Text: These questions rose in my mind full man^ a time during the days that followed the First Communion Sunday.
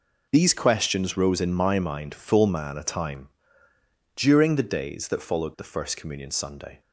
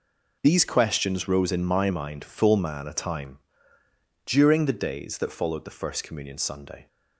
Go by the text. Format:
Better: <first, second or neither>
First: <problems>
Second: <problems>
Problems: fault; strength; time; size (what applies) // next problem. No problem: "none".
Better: neither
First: pauses between "time" and "during"; noticeable; at 3.2 s; 0.84 s long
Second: pauses between "time" and "during"; noticeable; at 3.3 s; 0.84 s long